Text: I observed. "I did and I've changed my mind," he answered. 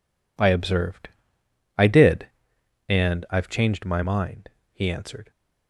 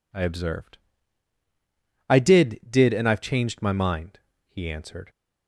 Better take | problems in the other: first | says "did" twice; at 2.6 s

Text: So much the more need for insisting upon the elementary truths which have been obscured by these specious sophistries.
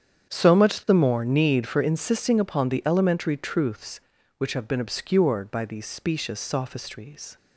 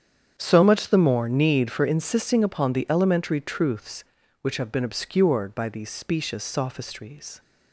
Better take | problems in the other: neither | starts louder than the rest; strong; the same in both

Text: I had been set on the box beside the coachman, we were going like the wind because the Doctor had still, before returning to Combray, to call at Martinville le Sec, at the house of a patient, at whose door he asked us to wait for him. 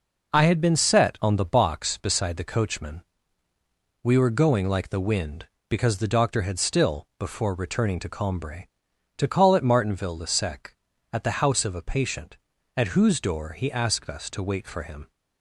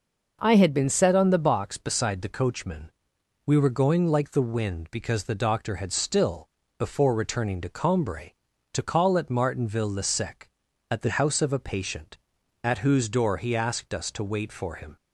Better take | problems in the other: neither | none

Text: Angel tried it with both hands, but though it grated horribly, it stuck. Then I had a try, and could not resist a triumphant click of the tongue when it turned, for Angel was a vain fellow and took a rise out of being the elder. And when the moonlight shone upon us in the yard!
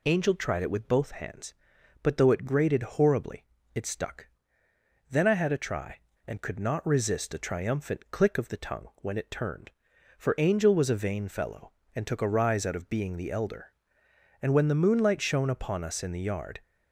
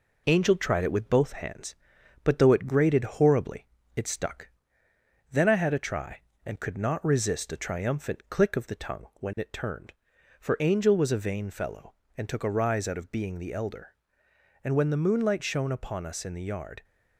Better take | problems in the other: first | gets quieter; slight; throughout; 2.5 dB

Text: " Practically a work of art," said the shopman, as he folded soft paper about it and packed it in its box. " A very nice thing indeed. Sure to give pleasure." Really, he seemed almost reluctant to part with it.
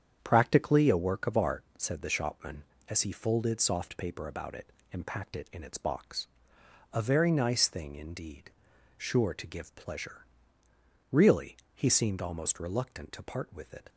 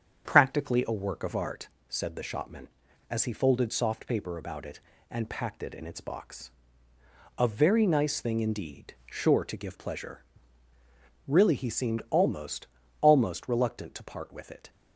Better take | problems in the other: first | starts louder than the rest; strong; until 1.3 s; 8 dB; strong in the first // says "almost" twice; at 13.0 s

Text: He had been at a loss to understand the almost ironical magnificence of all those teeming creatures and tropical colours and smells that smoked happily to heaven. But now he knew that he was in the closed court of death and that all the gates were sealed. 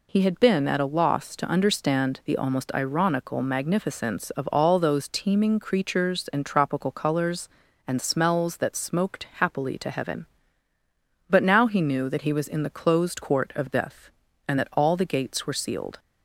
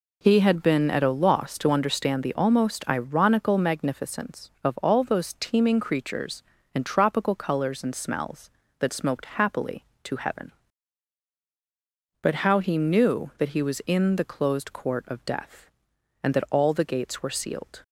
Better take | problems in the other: first | says "how" for "now"; at 12.4 s

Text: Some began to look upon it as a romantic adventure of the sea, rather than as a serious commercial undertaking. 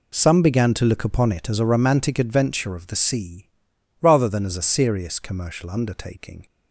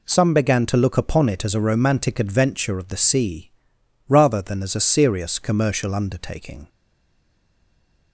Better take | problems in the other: first | stays silent after the last word; noticeable; from 6.6 s on; 1.5 s long

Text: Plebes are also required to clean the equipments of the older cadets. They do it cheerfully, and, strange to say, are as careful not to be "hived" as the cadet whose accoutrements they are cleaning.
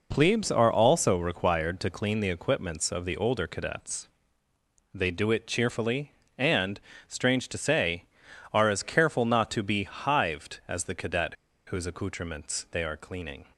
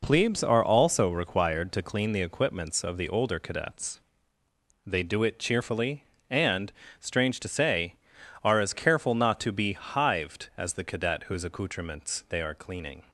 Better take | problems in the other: second | pauses between "cadet" and "whose"; slight; at 11.3 s; 0.31 s long

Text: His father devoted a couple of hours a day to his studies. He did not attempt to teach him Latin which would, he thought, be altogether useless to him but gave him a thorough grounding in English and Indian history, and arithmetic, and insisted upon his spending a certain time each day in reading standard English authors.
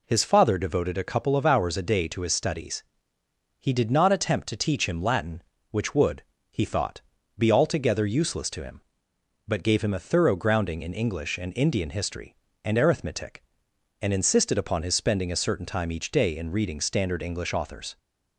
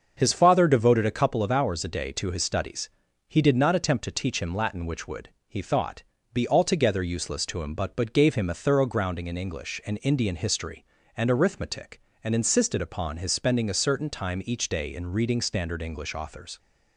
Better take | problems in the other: first | starts louder than the rest; until 1.1 s; 6.5 dB // says "but" twice; at 7.9 s

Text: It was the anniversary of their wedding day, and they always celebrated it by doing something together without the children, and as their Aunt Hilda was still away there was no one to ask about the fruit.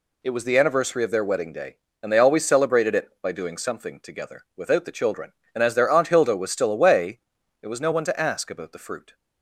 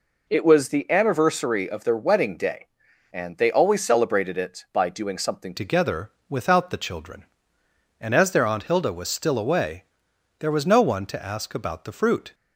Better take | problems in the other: first | changes voice at "together"; from 5.5 s on; 6.8 s long // pauses between "together" and "without"; slight; at 6.1 s; 0.16 s long // pauses between "away" and "there"; noticeable; at 9.8 s; 0.54 s long; also in the first

